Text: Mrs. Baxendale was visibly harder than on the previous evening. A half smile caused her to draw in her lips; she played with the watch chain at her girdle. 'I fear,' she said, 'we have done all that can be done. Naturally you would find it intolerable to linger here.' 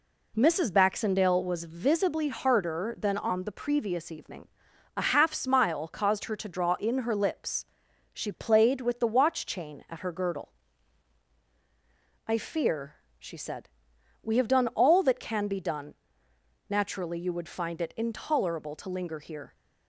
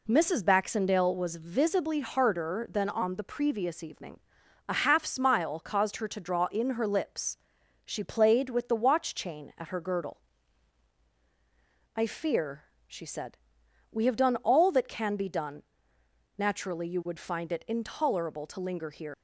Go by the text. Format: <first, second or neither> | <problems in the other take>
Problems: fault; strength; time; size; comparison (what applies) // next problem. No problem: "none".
first | leaves "here" unfinished; at 19.1 s; 110 ms